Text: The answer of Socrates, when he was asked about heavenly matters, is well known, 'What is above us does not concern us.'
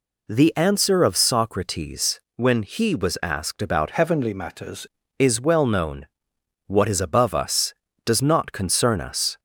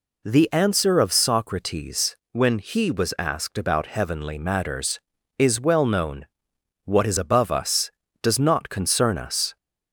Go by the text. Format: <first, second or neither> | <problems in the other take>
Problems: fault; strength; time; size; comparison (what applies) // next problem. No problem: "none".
second | changes voice from "heavenly" to "matters"; from 3.9 to 4.8 s; 0.9 s long